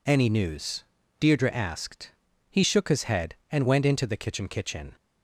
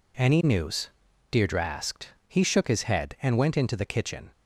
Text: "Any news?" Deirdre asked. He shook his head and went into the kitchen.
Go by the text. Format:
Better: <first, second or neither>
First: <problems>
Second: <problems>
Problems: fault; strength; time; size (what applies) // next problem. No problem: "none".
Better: second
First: says "kitchen" twice; at 4.4 s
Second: none